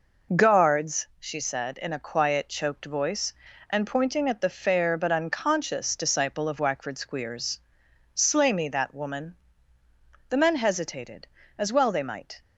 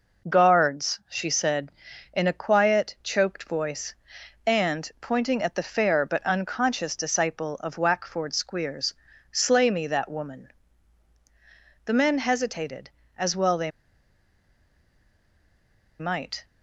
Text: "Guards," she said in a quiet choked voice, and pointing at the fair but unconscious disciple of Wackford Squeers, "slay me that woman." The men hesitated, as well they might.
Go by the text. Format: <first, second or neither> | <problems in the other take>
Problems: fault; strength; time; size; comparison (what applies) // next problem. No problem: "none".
first | pauses between "they" and "might"; strong; at 13.7 s; 2.2 s long